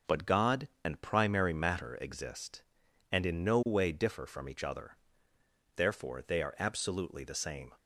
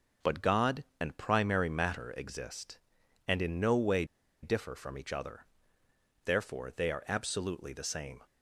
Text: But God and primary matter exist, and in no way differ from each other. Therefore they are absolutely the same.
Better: first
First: none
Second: pauses between "way" and "differ"; at 4.0 s; 0.38 s long

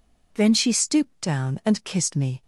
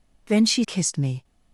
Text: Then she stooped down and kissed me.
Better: first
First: none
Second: skips "stooped down and"; at 0.6 s

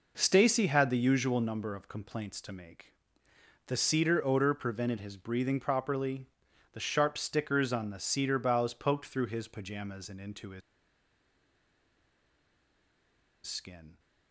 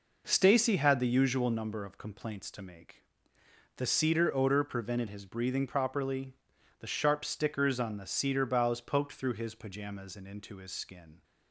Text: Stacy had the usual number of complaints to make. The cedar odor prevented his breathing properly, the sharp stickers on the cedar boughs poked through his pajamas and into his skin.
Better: second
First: pauses between "his" and "skin"; strong; at 10.6 s; 2.8 s long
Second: none

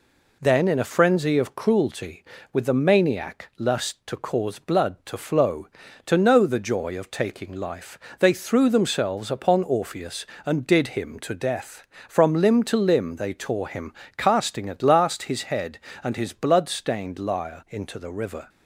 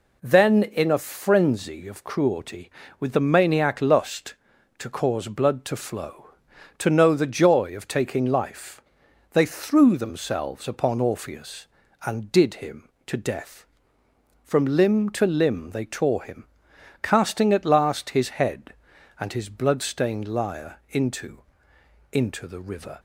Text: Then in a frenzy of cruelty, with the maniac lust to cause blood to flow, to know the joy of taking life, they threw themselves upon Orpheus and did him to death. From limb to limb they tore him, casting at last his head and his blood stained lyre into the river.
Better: first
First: none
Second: says "into" twice; at 22.1 s

